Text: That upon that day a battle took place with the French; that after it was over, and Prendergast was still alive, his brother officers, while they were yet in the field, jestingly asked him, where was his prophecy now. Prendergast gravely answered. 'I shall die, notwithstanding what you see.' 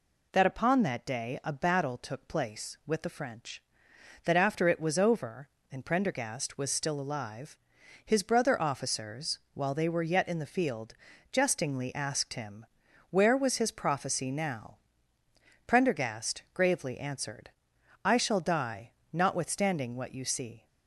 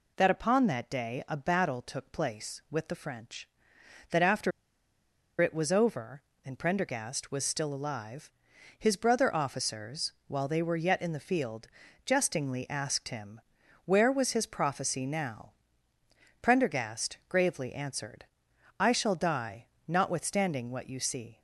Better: first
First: none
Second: pauses between "after" and "it"; noticeable; at 4.5 s; 0.90 s long

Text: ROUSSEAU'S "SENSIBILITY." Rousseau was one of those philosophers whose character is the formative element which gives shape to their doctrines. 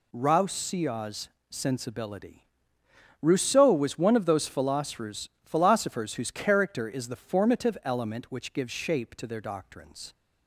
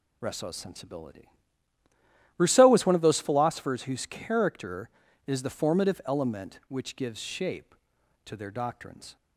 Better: second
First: pauses between "ROUSSEAU'S" and "SENSIBILITY"; slight; at 1.2 s; 0.22 s long // says "philosophers" twice; at 5.4 s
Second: none

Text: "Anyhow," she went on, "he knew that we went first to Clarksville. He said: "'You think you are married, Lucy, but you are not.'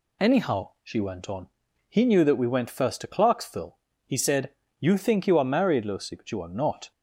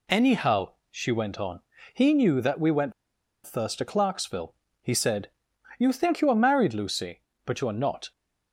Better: first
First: none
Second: pauses between "went" and "first"; noticeable; at 2.9 s; 0.52 s long

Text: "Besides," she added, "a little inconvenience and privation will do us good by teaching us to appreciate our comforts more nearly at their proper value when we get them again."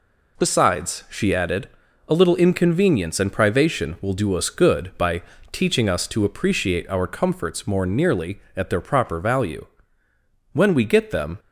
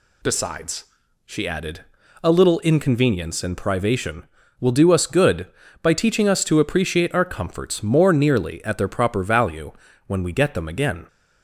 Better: second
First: pauses between "by" and "teaching"; slight; at 5.2 s; 0.30 s long // pauses between "value" and "when"; noticeable; at 9.6 s; 0.88 s long // stops before "again"; at 11.3 s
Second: pauses between "value" and "when"; slight; at 9.7 s; 0.34 s long

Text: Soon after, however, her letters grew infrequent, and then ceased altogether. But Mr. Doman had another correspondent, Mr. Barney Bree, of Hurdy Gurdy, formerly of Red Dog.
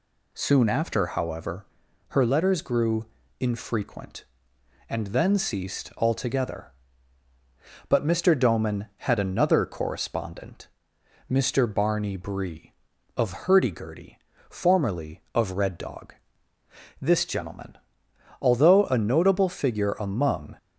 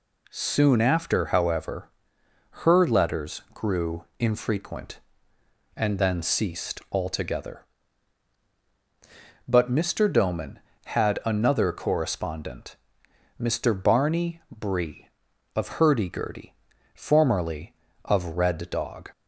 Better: second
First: pauses between "grew" and "infrequent"; slight; at 3.0 s; 0.34 s long // goes on to say "This gentleman although a notable figure among"; strong; from 16.9 s on; 3.5 s long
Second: none

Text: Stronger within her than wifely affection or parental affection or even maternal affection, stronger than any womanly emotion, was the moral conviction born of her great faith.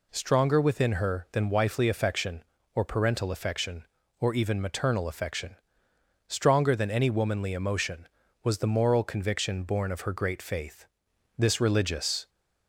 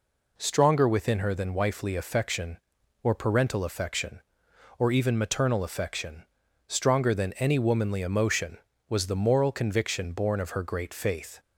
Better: second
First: goes on to say "This religious"; noticeable; from 11.3 s on; 0.92 s long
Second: none

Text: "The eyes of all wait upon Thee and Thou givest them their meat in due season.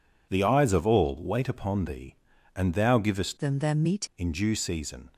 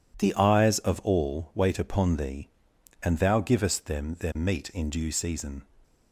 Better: second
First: changes voice from "them" to "meat"; from 3.3 to 4.0 s; 0.7 s long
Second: none

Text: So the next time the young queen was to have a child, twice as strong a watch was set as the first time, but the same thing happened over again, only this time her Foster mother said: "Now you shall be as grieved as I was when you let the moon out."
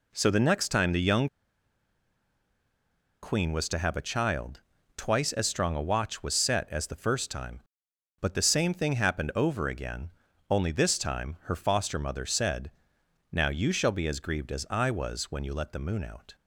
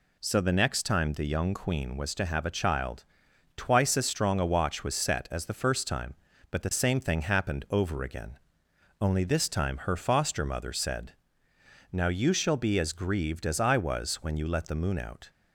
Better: second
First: pauses between "young" and "queen"; strong; at 1.2 s; 1.9 s long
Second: none

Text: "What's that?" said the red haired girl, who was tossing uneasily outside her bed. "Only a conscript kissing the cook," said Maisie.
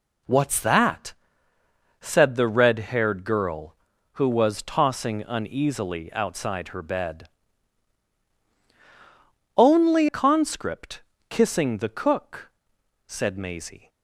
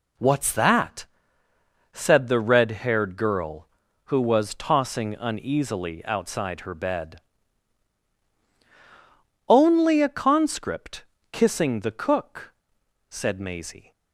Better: second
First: skips "a"; at 10.0 s // pauses between "conscript" and "kissing"; slight; at 11.0 s; 0.28 s long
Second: pauses between "conscript" and "kissing"; slight; at 11.0 s; 0.28 s long

